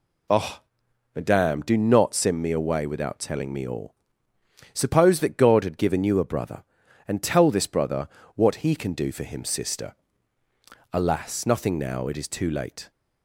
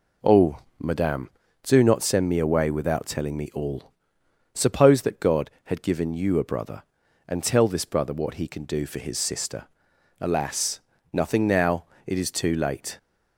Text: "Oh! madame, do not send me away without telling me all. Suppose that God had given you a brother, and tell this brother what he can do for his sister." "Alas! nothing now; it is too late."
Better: second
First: pauses between "brother" and "what"; slight; at 8.0 s; 0.28 s long // says "him" for "his"; at 9.2 s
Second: none

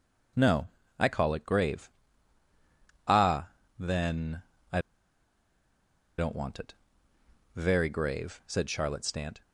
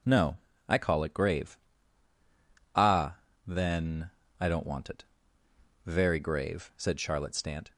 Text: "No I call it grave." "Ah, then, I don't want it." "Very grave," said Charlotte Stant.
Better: second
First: pauses between "No" and "I"; slight; at 0.6 s; 0.30 s long // pauses between "I" and "don't"; strong; at 4.8 s; 1.3 s long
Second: pauses between "No" and "I"; slight; at 0.3 s; 0.30 s long

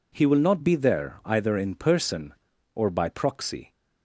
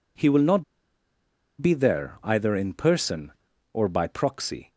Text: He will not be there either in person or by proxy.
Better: first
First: none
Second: pauses between "not" and "be"; noticeable; at 0.6 s; 0.96 s long

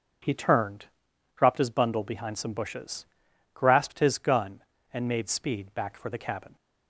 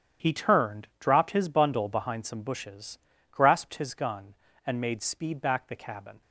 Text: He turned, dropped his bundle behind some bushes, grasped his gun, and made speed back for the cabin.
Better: first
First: starts louder than the rest; until 1.7 s; 7 dB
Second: starts louder than the rest; strong; until 1.3 s; 9.5 dB // skips "for"; at 5.6 s

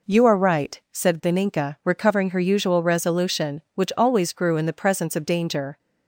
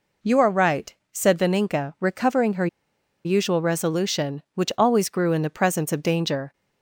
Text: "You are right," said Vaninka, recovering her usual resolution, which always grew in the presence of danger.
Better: first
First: none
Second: pauses between "her" and "usual"; noticeable; at 2.6 s; 0.58 s long

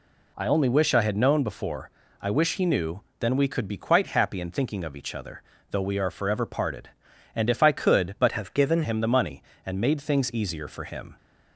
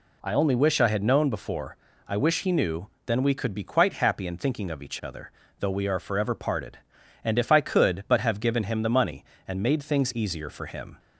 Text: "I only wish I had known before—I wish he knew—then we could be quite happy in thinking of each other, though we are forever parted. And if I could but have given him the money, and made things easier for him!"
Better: second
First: changes voice from "have" to "given"; from 8.3 to 8.8 s; 0.5 s long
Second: none

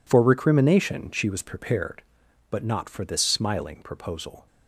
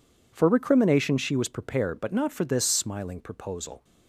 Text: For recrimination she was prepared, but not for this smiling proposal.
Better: neither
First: none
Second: none

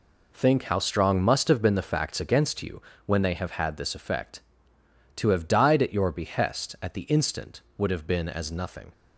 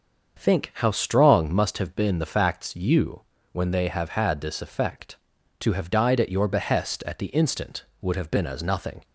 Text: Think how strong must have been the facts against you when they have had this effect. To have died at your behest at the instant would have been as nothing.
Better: first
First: pauses between "you" and "when"; slight; at 2.8 s; 0.24 s long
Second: starts louder than the rest; until 1.4 s; 6.5 dB // skips "against"; at 2.7 s // pauses between "you" and "when"; slight; at 3.2 s; 0.32 s long

